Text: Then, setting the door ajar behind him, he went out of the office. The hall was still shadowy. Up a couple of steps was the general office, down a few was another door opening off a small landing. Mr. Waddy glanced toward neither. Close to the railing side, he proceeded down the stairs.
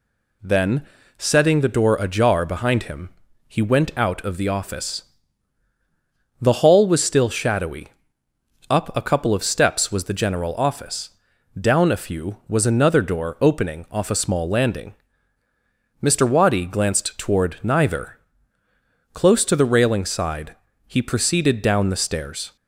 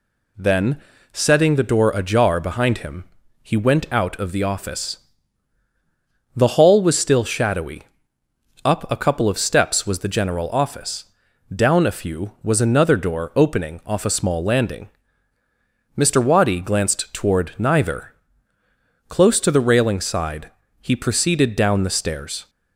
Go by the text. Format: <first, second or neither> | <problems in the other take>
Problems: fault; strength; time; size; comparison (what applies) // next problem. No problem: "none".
neither | none